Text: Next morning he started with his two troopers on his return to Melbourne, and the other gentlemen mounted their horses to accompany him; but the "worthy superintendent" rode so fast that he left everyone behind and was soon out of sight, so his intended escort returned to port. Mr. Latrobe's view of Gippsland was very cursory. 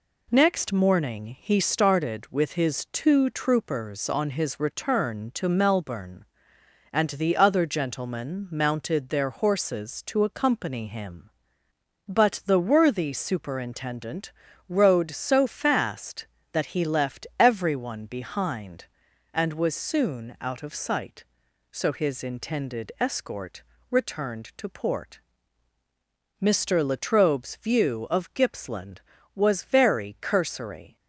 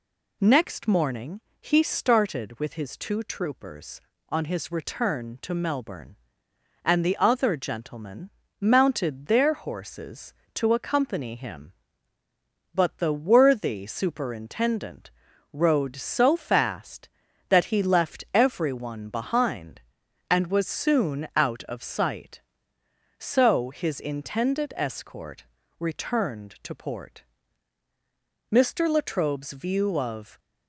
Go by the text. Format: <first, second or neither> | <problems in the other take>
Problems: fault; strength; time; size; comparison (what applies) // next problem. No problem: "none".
first | pauses between "morning" and "he"; slight; at 1.4 s; 0.20 s long // pauses between "gentlemen" and "mounted"; slight; at 8.2 s; 0.32 s long // pauses between "superintendent" and "rode"; noticeable; at 15.0 s; 0.46 s long; also in the first // pauses between "escort" and "returned"; slight; at 25.4 s; 0.34 s long; slight in the first // stops before "Gippsland was very cursory"; at 30.3 s